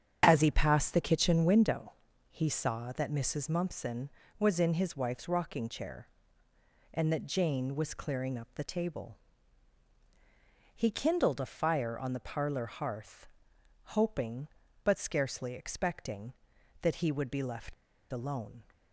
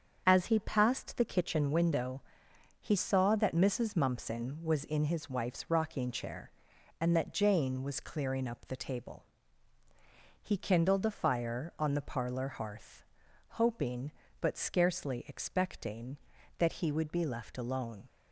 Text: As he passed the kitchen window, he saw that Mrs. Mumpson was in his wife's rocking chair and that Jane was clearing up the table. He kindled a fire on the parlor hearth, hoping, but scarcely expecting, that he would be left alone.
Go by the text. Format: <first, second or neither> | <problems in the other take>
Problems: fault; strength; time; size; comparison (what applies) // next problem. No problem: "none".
second | starts louder than the rest; strong; until 1.2 s; 7.5 dB; strong in the second // pauses between "left" and "alone"; at 17.7 s; 0.39 s long